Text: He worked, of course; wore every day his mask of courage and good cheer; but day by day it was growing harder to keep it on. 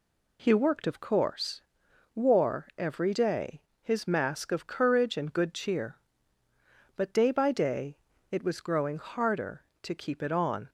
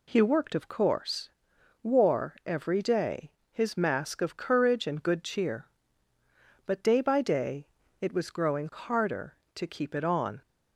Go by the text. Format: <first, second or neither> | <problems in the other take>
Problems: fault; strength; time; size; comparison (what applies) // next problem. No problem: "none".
neither | pauses between "day" and "his"; slight; the same in both // pauses between "day" and "it"; slight; the same in both